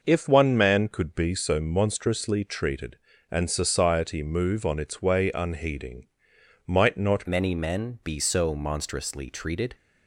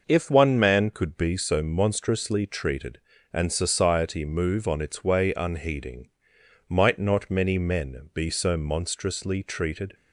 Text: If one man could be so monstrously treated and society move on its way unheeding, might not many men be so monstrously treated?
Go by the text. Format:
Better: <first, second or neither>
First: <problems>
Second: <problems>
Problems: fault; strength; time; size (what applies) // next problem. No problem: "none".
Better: second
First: changes voice at "many"; from 7.2 s on; 2.5 s long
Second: none